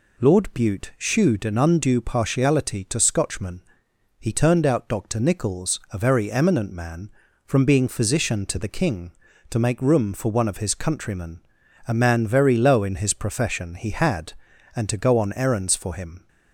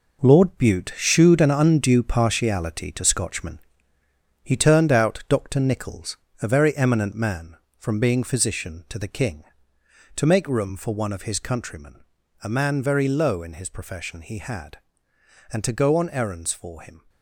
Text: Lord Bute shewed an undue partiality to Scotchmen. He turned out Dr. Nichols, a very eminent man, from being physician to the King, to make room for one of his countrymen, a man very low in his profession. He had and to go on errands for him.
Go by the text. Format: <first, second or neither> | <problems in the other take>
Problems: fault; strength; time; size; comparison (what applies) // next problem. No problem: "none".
first | gets quieter; strong; throughout; 8.5 dB